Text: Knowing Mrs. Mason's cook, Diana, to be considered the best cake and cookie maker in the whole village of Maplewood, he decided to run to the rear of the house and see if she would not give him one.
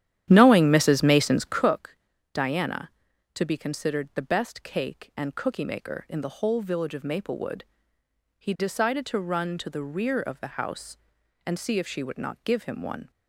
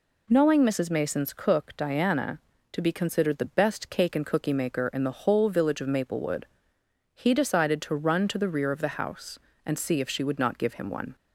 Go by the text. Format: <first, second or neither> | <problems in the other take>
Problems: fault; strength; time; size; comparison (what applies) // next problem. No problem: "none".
second | starts louder than the rest; strong; until 1.7 s; 11 dB